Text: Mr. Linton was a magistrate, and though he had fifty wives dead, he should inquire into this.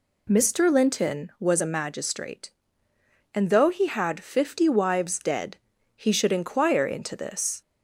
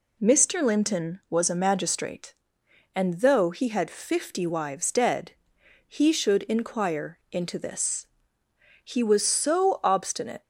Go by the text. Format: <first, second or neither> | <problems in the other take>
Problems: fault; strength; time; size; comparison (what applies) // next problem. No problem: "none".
first | goes on to say "He was so obstinate"; from 8.8 s on; 1.5 s long